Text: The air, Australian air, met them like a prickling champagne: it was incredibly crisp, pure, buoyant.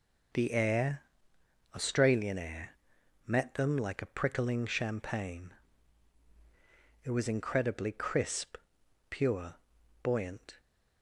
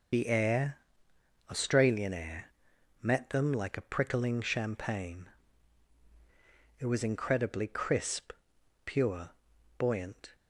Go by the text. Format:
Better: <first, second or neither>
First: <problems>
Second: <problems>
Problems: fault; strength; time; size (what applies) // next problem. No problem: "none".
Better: first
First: none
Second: loses the start of "The"; at 0.1 s; 35 ms